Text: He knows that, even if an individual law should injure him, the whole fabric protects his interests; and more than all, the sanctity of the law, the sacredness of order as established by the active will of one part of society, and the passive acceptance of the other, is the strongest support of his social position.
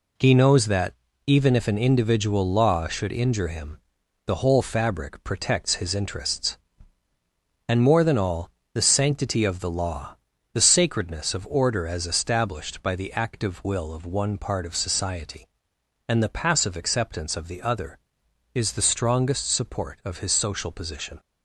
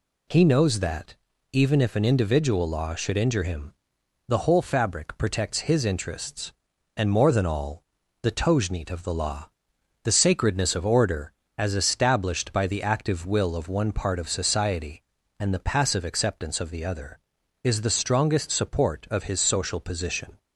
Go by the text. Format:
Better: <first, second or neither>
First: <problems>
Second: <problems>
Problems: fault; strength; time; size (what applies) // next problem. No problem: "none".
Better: first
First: none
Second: says "tojneet" for "sanctity"; at 8.3 s